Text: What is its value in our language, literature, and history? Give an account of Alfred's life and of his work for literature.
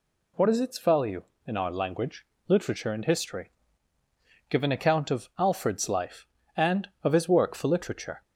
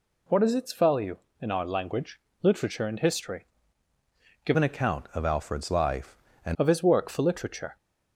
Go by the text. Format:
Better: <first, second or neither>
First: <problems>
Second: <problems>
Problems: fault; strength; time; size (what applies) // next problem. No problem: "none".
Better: first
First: none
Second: changes voice from "an" to "and"; from 4.5 to 6.5 s; 2.0 s long